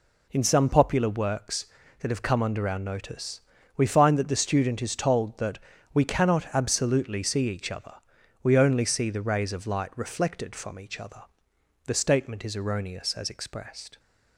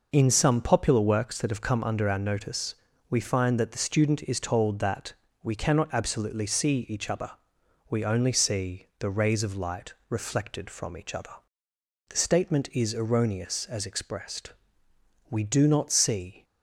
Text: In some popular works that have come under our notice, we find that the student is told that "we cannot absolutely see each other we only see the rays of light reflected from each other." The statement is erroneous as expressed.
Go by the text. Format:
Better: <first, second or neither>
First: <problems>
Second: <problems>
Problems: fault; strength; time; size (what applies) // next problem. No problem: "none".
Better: first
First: pauses between "that" and "we"; slight; at 5.5 s; 0.36 s long // pauses between "other" and "we"; noticeable; at 7.9 s; 0.48 s long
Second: pauses between "that" and "we"; slight; at 5.1 s; 0.28 s long // pauses between "other" and "we"; noticeable; at 7.3 s; 0.58 s long // goes on to say "We do not see"; noticeable; from 15.2 s on; 1.2 s long